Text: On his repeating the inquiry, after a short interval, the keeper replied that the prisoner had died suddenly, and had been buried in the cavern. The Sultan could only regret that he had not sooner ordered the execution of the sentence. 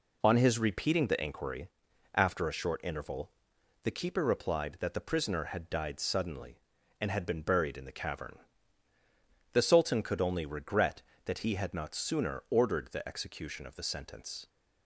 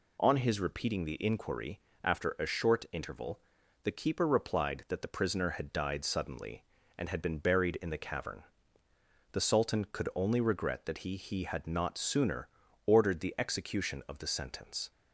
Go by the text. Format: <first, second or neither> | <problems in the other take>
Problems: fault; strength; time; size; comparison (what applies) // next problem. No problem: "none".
first | says "he" twice; at 11.1 s // pauses between "sooner" and "ordered"; at 12.4 s; 0.38 s long